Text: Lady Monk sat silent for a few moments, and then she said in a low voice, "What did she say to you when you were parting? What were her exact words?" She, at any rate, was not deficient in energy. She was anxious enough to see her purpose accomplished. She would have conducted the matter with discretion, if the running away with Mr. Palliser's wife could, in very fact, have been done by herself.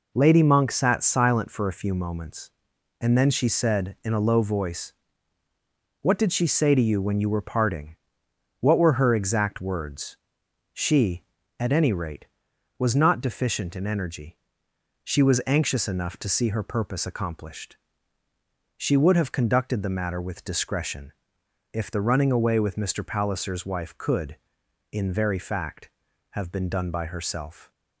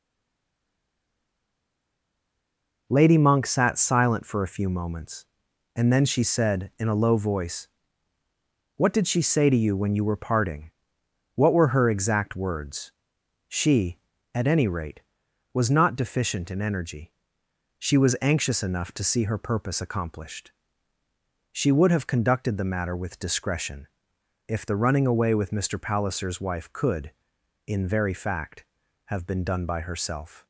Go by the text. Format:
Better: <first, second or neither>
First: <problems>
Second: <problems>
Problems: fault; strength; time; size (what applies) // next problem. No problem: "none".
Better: first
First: none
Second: stays silent before the first word; strong; until 2.8 s; 2.8 s long